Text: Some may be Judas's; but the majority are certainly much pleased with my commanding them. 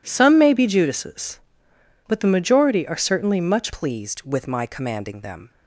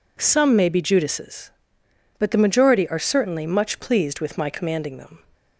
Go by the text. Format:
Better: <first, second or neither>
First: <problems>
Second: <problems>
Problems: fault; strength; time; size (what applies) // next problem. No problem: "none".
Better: second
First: changes voice at "pleased"; from 3.7 s on; 1.8 s long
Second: none